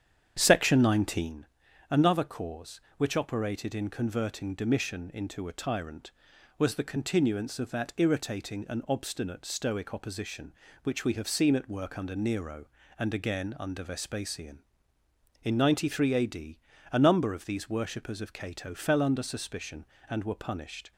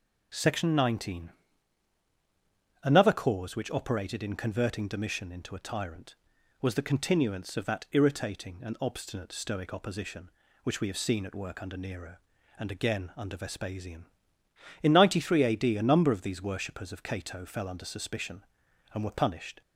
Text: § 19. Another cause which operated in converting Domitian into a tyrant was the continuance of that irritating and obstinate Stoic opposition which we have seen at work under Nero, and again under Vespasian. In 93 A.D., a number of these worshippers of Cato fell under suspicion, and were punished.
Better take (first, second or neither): second